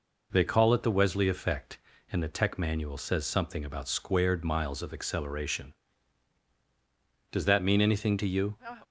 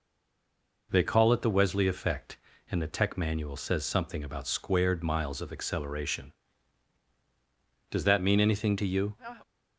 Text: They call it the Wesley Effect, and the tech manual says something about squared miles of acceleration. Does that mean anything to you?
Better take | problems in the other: first | stays silent before the first word; slight; until 0.8 s; 0.8 s long

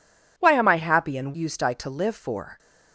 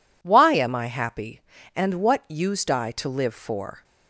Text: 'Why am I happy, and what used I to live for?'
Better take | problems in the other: second | skips "what"; at 1.3 s

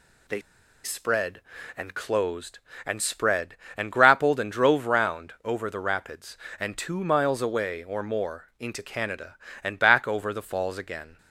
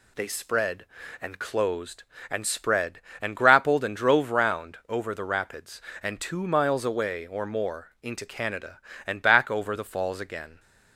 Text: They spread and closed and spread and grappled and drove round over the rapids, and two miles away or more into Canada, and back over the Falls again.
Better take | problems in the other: second | pauses between "They" and "spread"; at 0.4 s; 0.43 s long

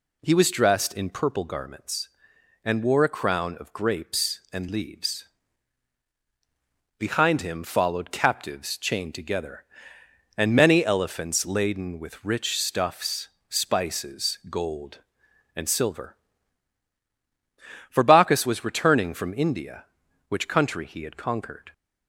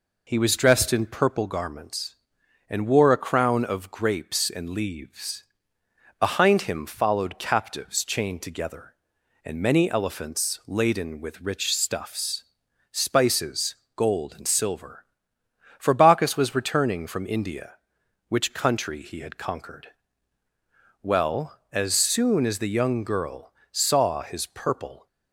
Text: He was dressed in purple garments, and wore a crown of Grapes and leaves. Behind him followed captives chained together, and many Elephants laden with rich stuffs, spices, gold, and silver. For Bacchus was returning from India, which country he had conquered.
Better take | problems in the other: first | goes on to say "Well as soon as the young girl saw his purple"; strong; from 21.0 s on; 4.0 s long

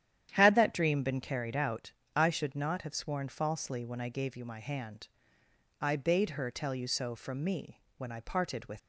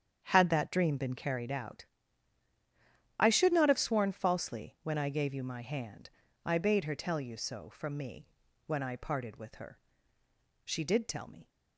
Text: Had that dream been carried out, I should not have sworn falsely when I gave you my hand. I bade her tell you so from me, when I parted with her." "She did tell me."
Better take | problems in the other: second | starts louder than the rest; strong; until 1.3 s; 10.5 dB; strong in the second // stops before "her She did tell me"; at 8.7 s

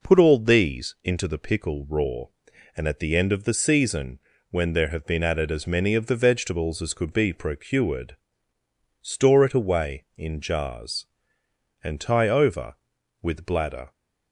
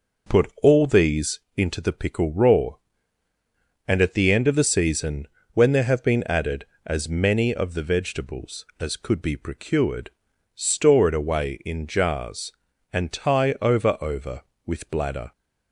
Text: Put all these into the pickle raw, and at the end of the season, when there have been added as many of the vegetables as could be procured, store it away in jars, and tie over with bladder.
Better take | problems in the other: first | pauses between "these" and "into"; slight; at 1.3 s; 0.16 s long // says "over" twice; at 14.0 s

